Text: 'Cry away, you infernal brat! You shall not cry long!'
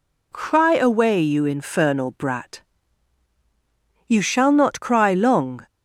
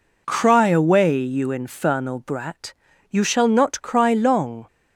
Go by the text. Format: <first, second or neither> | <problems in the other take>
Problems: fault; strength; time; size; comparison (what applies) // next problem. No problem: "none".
neither | none